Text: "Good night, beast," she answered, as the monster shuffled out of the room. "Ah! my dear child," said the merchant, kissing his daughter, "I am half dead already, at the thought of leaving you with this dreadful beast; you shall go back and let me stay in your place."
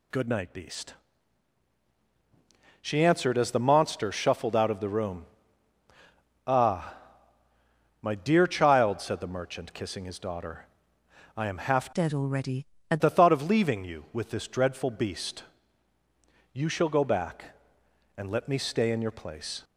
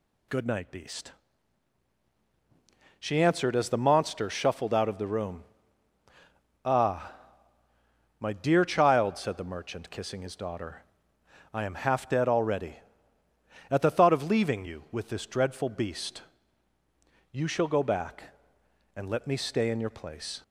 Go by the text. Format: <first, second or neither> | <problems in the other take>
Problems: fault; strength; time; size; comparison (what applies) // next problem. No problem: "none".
second | changes voice from "dead" to "at"; from 11.9 to 13.0 s; 1.1 s long